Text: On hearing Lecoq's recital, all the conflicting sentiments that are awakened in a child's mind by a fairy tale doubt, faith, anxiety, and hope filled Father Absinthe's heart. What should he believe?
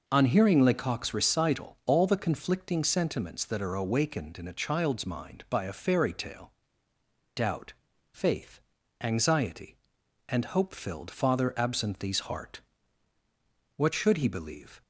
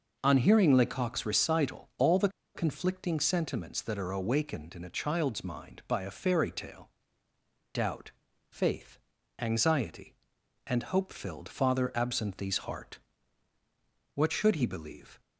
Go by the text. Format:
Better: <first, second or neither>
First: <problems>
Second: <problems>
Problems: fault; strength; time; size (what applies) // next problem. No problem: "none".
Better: first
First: pauses between "tale" and "doubt"; noticeable; at 6.5 s; 0.84 s long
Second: pauses between "the" and "conflicting"; slight; at 2.2 s; 0.26 s long // pauses between "tale" and "doubt"; noticeable; at 6.8 s; 0.84 s long